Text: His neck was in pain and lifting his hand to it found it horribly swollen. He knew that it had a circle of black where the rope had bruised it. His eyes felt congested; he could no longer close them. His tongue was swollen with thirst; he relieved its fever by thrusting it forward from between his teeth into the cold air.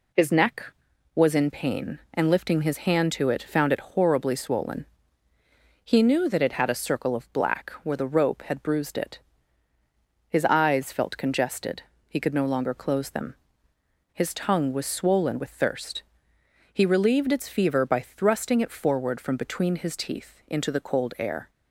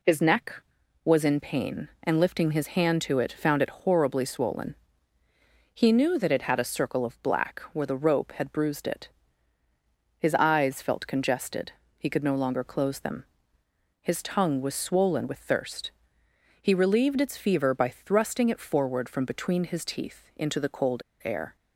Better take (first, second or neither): first